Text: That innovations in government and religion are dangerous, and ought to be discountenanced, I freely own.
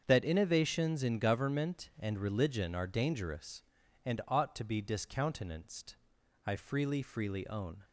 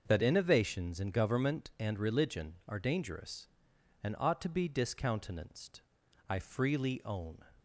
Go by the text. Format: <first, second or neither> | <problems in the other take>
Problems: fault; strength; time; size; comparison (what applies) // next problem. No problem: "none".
second | starts louder than the rest; until 1.0 s; 7 dB; also in the second // says "freely" twice; at 7.0 s